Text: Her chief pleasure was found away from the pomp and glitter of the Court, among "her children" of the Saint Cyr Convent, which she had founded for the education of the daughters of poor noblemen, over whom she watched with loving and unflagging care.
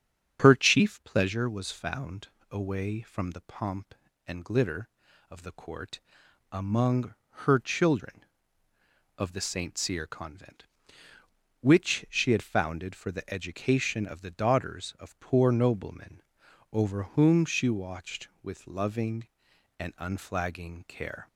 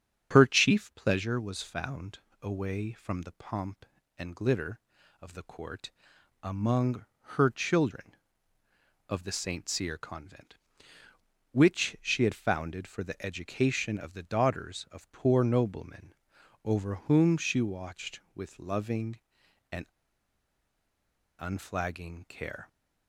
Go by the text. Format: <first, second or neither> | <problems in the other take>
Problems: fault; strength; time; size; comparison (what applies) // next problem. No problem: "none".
first | starts louder than the rest; strong; until 1.3 s; 8 dB; strong in the first // pauses between "found" and "away"; slight; at 2.1 s; 0.22 s long; slight in the first // pauses between "among" and "her"; slight; at 7.0 s; 0.32 s long; slight in the first // pauses between "and" and "unflagging"; strong; at 19.8 s; 1.5 s long